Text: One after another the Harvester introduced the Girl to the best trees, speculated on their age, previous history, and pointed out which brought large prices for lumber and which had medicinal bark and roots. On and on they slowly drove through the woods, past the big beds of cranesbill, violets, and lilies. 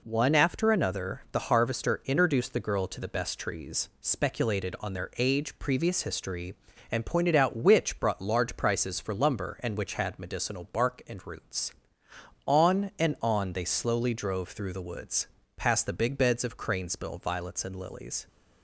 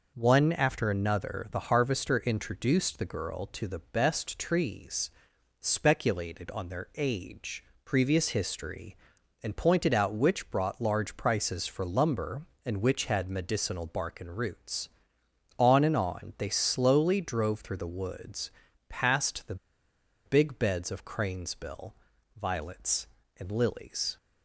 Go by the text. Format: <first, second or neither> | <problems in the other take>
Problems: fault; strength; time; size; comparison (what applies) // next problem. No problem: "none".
first | pauses between "the" and "big"; noticeable; at 19.5 s; 0.70 s long